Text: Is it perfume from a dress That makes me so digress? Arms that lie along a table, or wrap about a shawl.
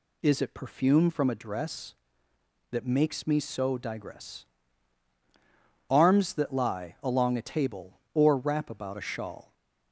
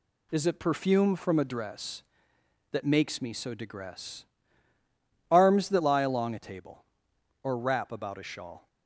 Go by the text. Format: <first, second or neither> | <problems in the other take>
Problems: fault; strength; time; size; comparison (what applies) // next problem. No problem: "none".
neither | none